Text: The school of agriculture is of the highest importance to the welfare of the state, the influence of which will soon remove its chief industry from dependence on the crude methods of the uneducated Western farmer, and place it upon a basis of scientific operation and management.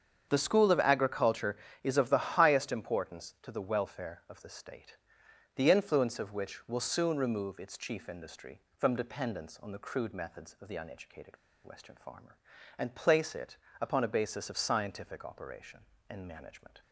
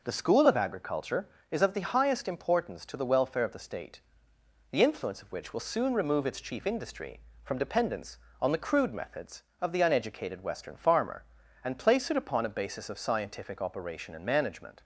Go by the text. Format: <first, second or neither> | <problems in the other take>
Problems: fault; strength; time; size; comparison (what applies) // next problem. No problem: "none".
second | starts louder than the rest; strong; until 1.3 s; 7.5 dB // pauses between "uneducated" and "Western"; slight; at 11.3 s; 0.28 s long // pauses between "it" and "upon"; slight; at 13.5 s; 0.24 s long